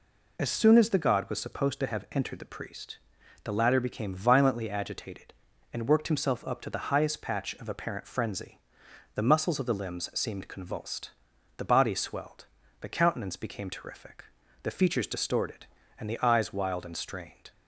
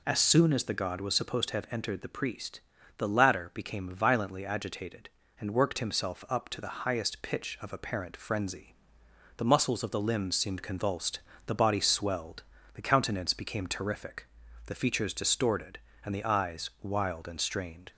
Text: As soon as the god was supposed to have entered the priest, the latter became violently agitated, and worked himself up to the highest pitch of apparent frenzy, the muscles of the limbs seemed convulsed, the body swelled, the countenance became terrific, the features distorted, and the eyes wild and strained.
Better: second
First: says "patch" for "pitch"; at 7.2 s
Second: none

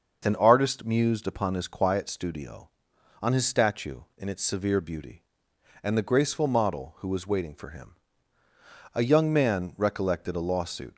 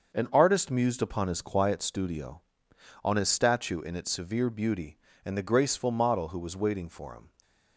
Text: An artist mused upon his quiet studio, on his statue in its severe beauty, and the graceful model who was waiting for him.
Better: second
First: starts louder than the rest; noticeable; until 1.2 s; 6 dB // goes on to say "A young man recollected a lawsuit"; strong; from 8.9 s on; 2.0 s long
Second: starts louder than the rest; until 1.1 s; 6.5 dB

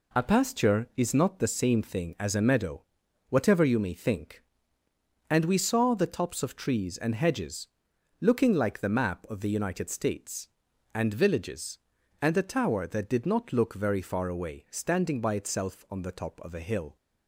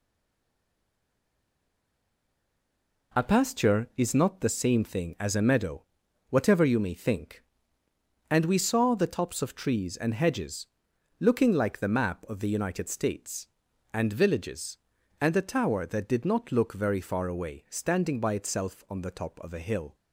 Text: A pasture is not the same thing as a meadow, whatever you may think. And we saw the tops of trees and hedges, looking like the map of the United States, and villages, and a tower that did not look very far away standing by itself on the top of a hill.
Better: first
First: none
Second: stays silent before the first word; strong; until 3.1 s; 3.1 s long

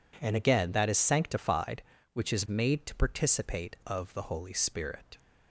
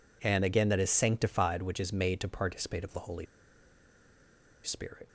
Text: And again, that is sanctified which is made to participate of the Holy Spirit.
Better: first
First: none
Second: pauses between "Holy" and "Spirit"; strong; at 3.2 s; 1.3 s long

